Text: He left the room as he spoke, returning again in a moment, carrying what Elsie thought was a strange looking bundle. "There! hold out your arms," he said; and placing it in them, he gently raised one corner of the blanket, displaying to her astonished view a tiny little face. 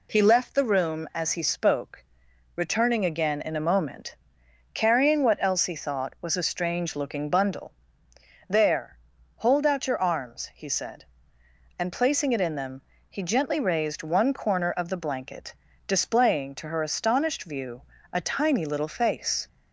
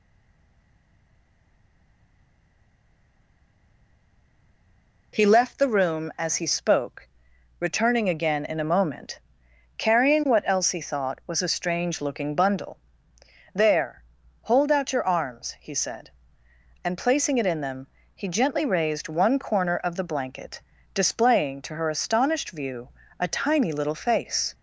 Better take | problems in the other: first | stays silent before the first word; strong; until 5.1 s; 5.1 s long // pauses between "view" and "a"; slight; at 22.8 s; 0.28 s long; slight in the first

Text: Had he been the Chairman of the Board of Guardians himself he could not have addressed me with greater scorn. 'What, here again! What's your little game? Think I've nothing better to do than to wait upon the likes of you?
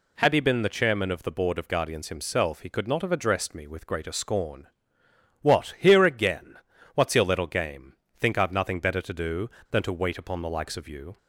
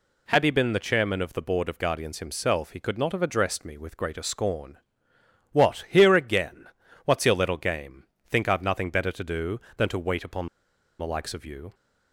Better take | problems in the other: first | pauses between "upon" and "the"; noticeable; at 10.4 s; 0.51 s long

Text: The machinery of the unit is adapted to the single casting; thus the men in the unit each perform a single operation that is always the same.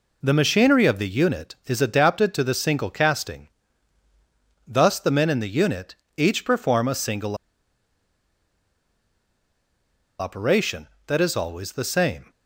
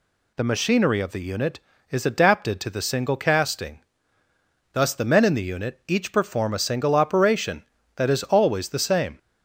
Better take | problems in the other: second | pauses between "unit" and "each"; slight; at 5.9 s; 0.20 s long // pauses between "single" and "operation"; strong; at 7.3 s; 2.8 s long

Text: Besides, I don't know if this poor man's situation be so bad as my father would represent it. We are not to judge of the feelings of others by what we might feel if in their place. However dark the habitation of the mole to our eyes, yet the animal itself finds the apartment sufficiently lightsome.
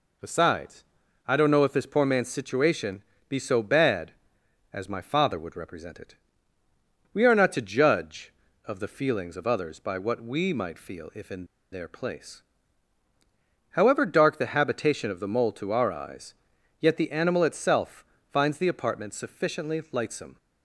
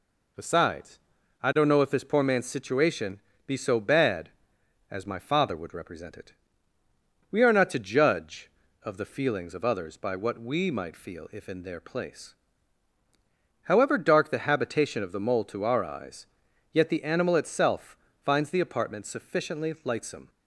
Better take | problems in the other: second | pauses between "situation" and "be"; slight; at 3.0 s; 0.24 s long; slight in the second // pauses between "in" and "their"; slight; at 11.4 s; 0.26 s long // pauses between "itself" and "finds"; slight; at 18.0 s; 0.26 s long; slight in the second

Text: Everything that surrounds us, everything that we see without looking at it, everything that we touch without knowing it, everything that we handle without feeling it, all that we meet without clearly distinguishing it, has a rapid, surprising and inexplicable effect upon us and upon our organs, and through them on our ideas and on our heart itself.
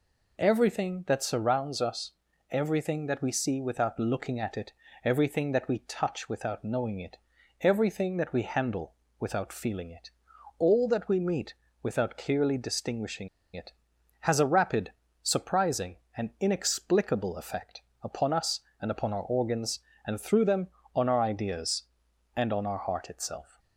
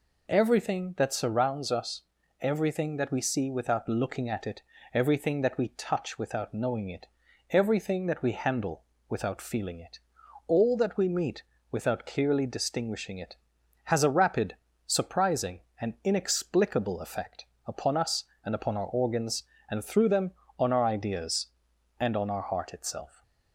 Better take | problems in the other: second | pauses between "handle" and "without"; slight; at 8.9 s; 0.26 s long; slight in the second // pauses between "meet" and "without"; slight; at 11.5 s; 0.28 s long; slight in the second // pauses between "distinguishing" and "it"; slight; at 13.2 s; 0.26 s long // pauses between "effect" and "upon"; slight; at 17.8 s; 0.22 s long; slight in the second

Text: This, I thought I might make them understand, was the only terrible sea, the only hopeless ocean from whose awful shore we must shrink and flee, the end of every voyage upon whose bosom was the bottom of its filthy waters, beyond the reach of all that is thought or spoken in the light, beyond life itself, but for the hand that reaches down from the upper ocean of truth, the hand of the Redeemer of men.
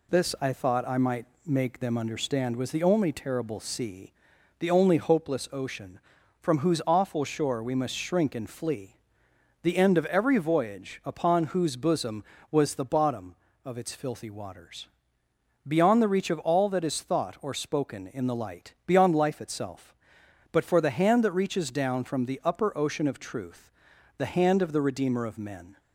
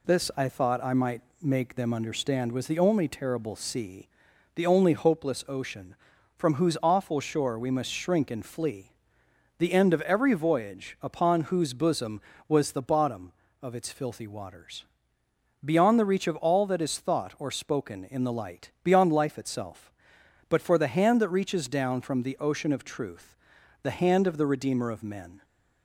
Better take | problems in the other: first | pauses between "might" and "make"; slight; at 1.2 s; 0.20 s long; slight in the first // skips "upper"; at 22.3 s

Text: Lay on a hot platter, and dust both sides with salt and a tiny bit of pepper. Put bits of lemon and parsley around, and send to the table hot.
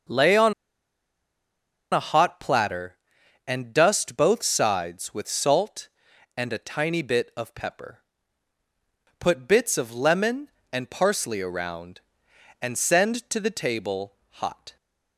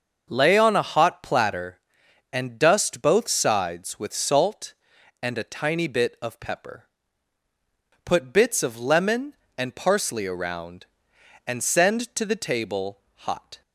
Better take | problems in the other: second | starts louder than the rest; until 2.5 s; 6 dB; also in the second // pauses between "on" and "a"; strong; at 0.5 s; 1.4 s long // pauses between "table" and "hot"; slight; at 14.1 s; 0.16 s long; slight in the second

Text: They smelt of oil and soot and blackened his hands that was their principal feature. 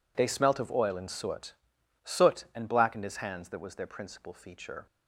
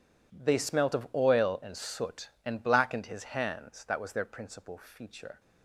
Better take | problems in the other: second | says "soot" twice; at 2.0 s

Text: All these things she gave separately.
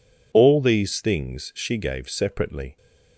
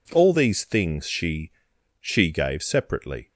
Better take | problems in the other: first | says "she" twice; at 2.0 s

